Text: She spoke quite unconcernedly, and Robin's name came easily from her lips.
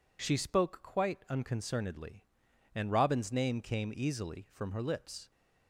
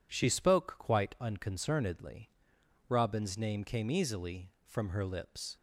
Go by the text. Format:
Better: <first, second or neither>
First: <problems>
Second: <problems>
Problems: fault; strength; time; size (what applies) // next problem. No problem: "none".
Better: first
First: none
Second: skips "and"; at 2.5 s